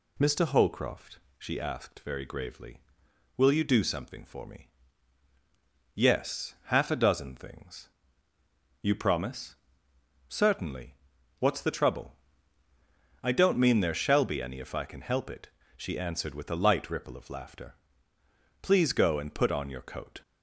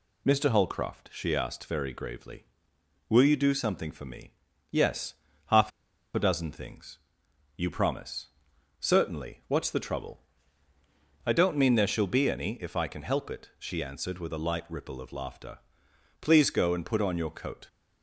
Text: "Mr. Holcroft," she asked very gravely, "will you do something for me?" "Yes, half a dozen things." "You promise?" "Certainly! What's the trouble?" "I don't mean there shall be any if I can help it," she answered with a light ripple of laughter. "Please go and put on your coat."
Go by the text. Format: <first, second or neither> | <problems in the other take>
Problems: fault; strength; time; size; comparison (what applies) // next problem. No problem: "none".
first | pauses between "half" and "a"; at 5.7 s; 0.44 s long